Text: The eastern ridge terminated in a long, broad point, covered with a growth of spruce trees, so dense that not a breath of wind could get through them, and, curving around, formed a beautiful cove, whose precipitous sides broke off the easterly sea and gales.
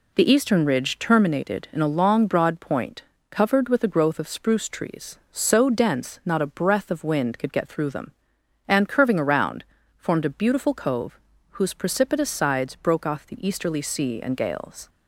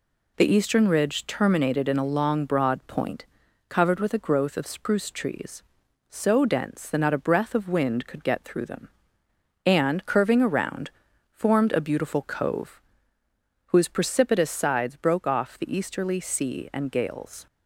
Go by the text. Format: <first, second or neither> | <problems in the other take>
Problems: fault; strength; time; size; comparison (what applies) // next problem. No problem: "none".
second | skips "that"; at 6.2 s